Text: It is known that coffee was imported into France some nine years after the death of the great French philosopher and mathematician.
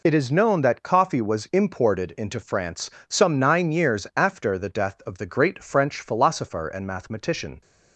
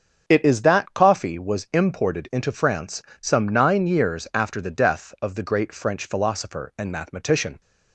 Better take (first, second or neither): first